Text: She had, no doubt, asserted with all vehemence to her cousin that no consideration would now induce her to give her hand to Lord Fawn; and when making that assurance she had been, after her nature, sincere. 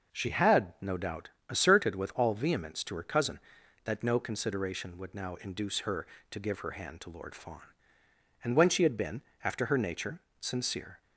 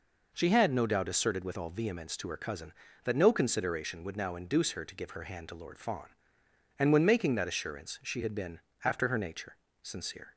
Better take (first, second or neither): second